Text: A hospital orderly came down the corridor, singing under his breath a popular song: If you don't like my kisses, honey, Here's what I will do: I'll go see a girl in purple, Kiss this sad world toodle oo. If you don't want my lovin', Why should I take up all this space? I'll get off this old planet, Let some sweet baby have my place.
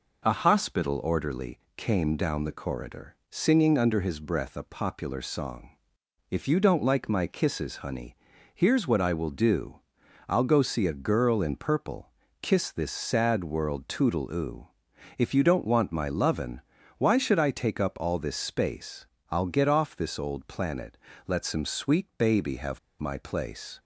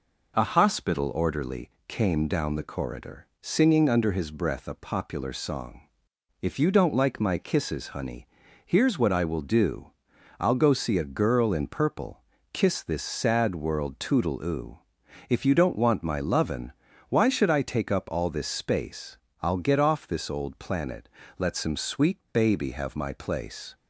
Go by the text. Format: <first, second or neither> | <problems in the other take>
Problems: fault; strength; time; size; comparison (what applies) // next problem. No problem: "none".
second | pauses between "orderly" and "came"; slight; at 1.5 s; 0.18 s long; slight in the second // pauses between "have" and "my"; slight; at 22.7 s; 0.20 s long